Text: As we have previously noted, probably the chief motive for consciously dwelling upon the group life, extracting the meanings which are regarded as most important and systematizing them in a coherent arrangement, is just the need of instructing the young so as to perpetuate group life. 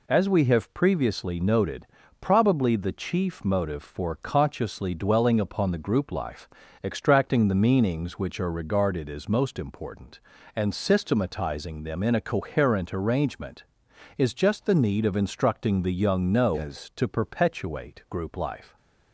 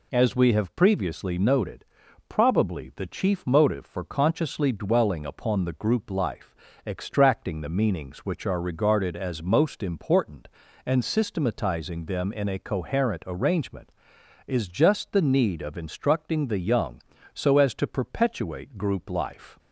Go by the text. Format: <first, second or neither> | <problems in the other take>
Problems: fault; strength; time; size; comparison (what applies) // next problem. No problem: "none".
second | says "no" for "so"; at 16.2 s